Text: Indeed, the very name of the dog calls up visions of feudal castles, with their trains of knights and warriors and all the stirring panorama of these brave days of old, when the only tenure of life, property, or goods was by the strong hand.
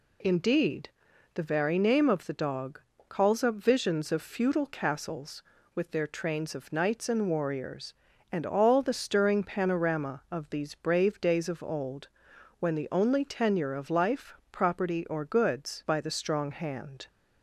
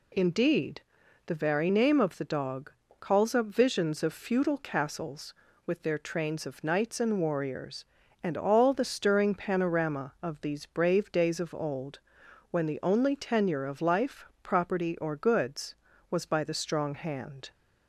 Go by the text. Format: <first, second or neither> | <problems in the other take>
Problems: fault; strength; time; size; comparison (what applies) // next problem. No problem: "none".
second | pauses between "dog" and "calls"; slight; at 2.7 s; 0.30 s long; slight in the second // skips "was"; at 15.8 s